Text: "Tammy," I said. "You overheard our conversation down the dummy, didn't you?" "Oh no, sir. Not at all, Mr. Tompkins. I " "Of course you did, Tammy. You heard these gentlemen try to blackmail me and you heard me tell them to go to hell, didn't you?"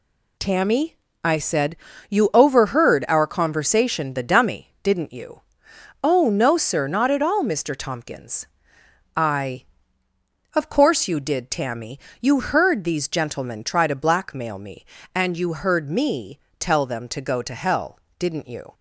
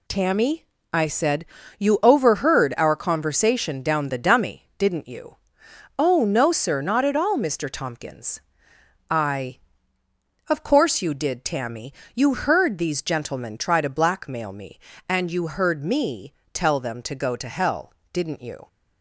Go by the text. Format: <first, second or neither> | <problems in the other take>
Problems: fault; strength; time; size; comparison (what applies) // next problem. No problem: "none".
second | skips "down"; at 4.1 s // pauses between "me" and "tell"; slight; at 16.3 s; 0.20 s long; slight in the second